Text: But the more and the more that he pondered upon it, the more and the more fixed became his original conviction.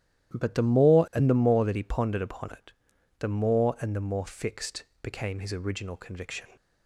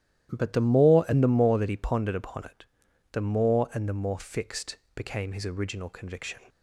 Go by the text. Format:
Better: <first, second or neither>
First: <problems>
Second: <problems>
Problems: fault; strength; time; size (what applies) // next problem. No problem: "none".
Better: neither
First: starts louder than the rest; strong; until 1.4 s; 12 dB // pauses between "fixed" and "became"; slight; at 4.8 s; 0.16 s long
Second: starts louder than the rest; strong; until 1.3 s; 12 dB // pauses between "fixed" and "became"; slight; at 4.7 s; 0.16 s long